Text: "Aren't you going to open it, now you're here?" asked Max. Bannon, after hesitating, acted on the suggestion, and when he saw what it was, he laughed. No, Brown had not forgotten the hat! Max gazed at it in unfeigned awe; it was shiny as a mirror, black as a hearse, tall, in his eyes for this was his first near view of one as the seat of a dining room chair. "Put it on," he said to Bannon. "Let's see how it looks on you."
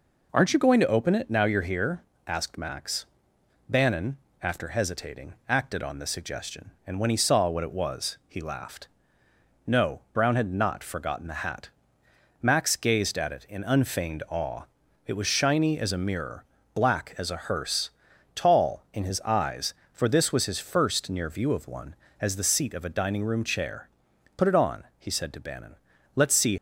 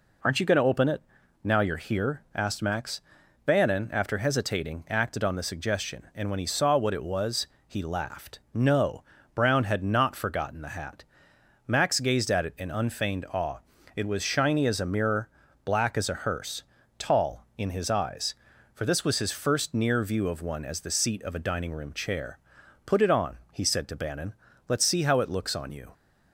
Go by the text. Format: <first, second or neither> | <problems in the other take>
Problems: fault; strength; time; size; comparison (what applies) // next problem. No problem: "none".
second | stops before "how it looks on you"; at 26.5 s